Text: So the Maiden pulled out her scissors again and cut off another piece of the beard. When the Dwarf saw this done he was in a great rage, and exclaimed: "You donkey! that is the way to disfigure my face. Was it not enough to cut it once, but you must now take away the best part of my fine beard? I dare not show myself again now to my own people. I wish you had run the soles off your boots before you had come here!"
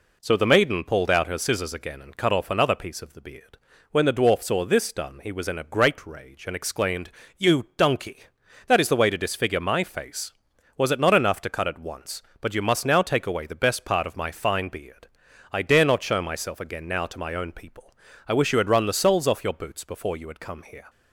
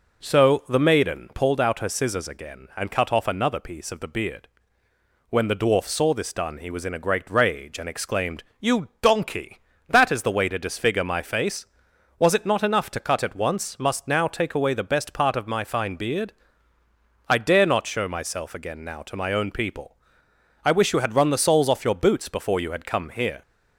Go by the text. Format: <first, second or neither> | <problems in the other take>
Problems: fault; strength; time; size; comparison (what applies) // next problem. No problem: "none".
first | skips "but you"; at 13.7 s